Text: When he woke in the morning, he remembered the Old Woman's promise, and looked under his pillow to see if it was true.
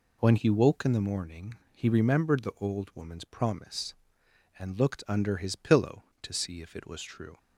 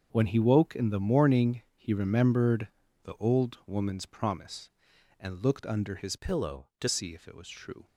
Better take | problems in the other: first | starts louder than the rest; until 1.1 s; 6.5 dB // pauses between "remembered" and "the"; at 2.6 s; 0.38 s long // changes voice from "pillow" to "to"; from 6.1 to 6.8 s; 0.7 s long

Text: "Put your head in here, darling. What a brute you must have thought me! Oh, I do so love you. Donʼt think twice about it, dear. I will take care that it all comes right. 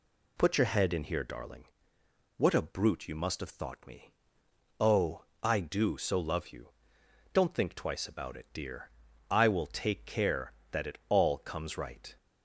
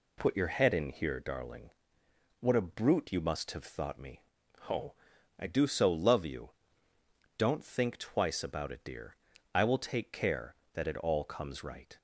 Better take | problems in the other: neither | none

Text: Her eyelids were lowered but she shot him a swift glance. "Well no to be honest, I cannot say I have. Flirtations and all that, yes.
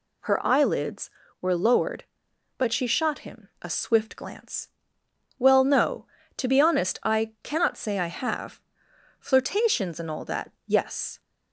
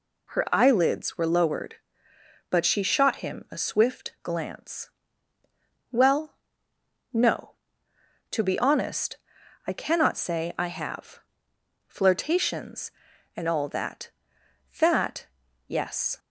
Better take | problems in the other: first | pauses between "Well" and "no"; noticeable; at 6.3 s; 0.78 s long // says "that" twice; at 14.8 s

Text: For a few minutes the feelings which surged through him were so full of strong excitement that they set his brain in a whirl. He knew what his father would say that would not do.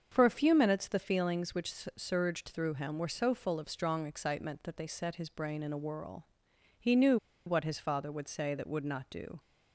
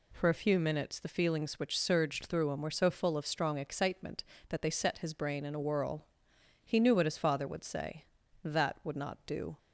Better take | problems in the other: second | starts louder than the rest; until 1.1 s; 7 dB // pauses between "which" and "surged"; slight; at 1.7 s; 0.24 s long // pauses between "knew" and "what"; slight; at 7.1 s; 0.29 s long

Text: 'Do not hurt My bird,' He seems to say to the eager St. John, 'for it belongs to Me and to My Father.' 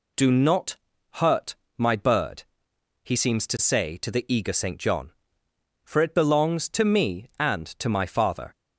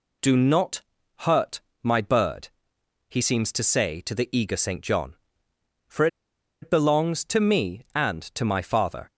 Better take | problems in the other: first | pauses between "not" and "hurt"; at 0.8 s; 0.40 s long; also in the first // pauses between "hurt" and "My"; slight; at 1.6 s; 0.22 s long; slight in the first // pauses between "for" and "it"; noticeable; at 6.0 s; 0.57 s long

